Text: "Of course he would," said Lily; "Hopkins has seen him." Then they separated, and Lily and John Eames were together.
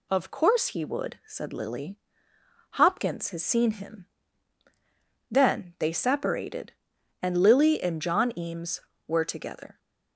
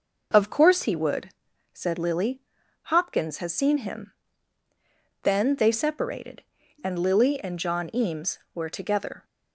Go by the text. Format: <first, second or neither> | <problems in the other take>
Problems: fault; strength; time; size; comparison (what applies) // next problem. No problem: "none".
neither | none